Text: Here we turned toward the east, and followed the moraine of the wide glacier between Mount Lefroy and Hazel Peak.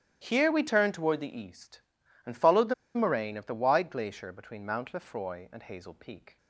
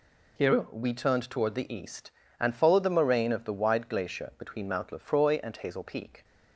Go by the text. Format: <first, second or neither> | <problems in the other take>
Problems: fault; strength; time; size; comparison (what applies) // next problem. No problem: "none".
second | starts louder than the rest; strong; until 1.2 s; 12 dB // pauses between "the" and "moraine"; slight; at 2.7 s; 0.22 s long